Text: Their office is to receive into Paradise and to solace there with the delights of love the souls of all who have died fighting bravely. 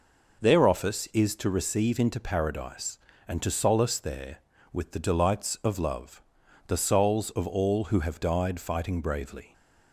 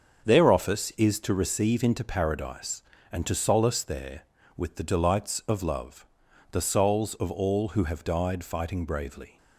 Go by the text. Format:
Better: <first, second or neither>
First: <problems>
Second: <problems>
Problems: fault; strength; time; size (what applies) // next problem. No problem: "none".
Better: first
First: pauses between "love" and "the"; noticeable; at 6.2 s; 0.46 s long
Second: gets quieter; strong; throughout; 7.5 dB // pauses between "love" and "the"; noticeable; at 6.0 s; 0.46 s long